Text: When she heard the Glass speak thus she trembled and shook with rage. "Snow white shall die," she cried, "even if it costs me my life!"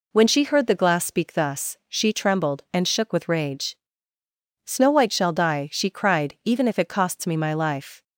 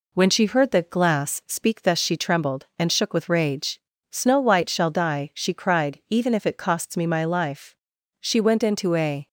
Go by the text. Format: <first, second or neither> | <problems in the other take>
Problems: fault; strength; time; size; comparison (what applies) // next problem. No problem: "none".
first | goes on to say "She went into a"; noticeable; from 8.2 s on; 1.0 s long